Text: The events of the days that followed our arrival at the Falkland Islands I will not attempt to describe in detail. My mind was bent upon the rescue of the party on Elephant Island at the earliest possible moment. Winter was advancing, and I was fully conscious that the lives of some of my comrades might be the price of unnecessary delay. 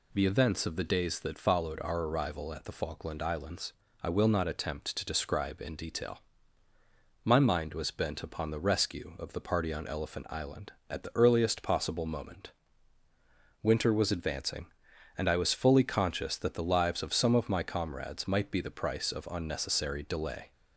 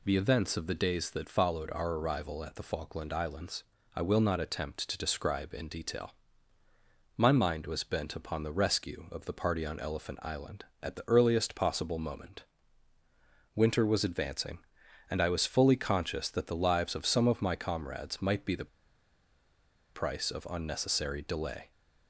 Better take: first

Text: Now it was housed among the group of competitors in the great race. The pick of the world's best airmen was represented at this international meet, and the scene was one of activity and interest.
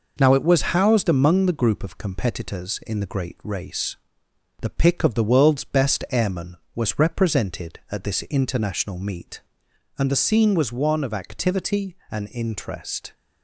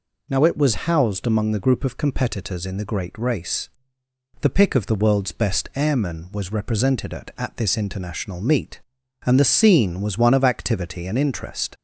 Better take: first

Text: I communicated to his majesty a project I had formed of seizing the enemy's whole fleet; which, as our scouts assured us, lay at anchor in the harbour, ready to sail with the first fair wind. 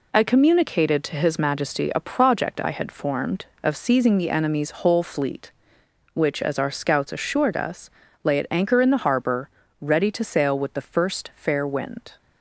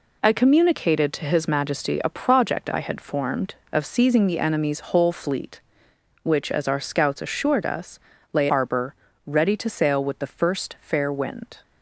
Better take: first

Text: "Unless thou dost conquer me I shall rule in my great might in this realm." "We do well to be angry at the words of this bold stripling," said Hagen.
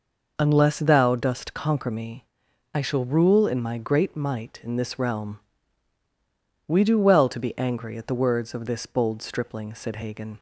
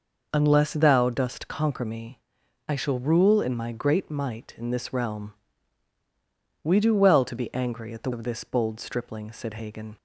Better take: first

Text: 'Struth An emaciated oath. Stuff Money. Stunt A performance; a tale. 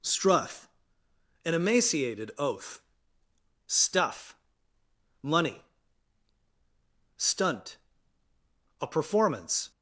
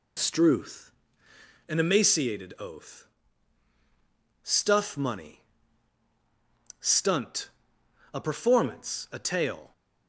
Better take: second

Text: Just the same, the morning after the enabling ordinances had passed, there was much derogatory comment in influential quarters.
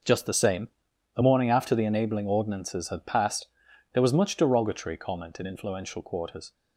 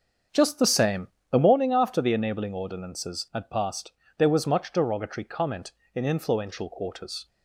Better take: first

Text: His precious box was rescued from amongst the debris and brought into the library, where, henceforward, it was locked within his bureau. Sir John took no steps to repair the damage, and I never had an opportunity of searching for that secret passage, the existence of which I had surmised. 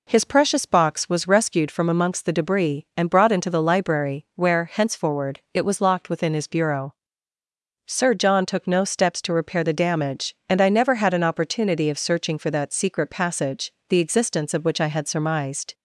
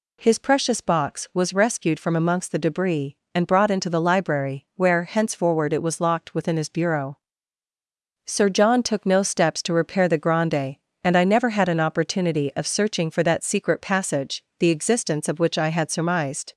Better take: first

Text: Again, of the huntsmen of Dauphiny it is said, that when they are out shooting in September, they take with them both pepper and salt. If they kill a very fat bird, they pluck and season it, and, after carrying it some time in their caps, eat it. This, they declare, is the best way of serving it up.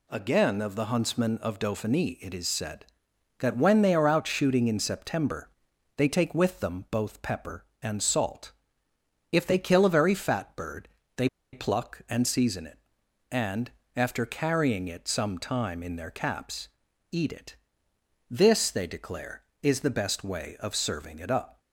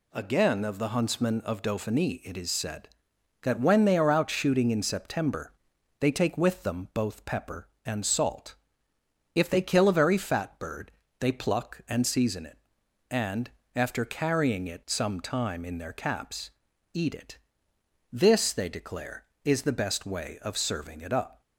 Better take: second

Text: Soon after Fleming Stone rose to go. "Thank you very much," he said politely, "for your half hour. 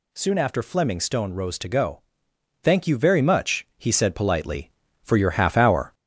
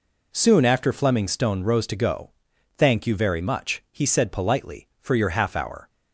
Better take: second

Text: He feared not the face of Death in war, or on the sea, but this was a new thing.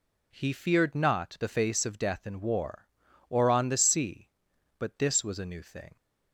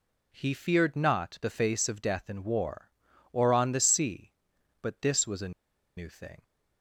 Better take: first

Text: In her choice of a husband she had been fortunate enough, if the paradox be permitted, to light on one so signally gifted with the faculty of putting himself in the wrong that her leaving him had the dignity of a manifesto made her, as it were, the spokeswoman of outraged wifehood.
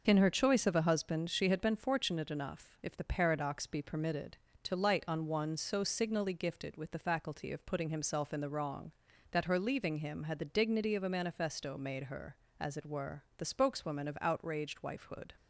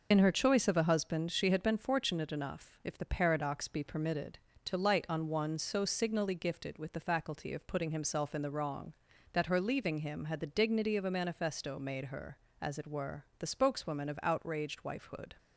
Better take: first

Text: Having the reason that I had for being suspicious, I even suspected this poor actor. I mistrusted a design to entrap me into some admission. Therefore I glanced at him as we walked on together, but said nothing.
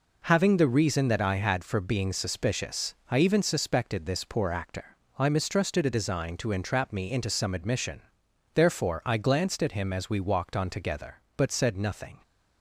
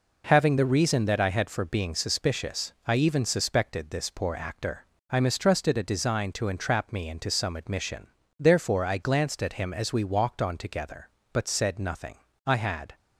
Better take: first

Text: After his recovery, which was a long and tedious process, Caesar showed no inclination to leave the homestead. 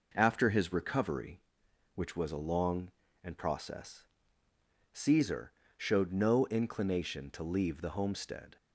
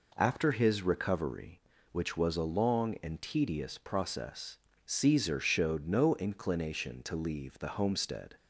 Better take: second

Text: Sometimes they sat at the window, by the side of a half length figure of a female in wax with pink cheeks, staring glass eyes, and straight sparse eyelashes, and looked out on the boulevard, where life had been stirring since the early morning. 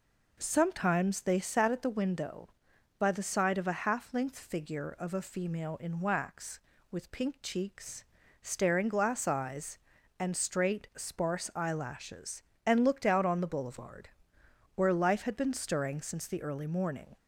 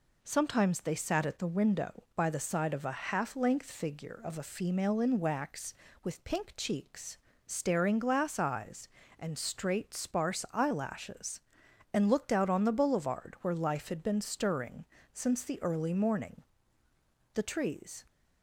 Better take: first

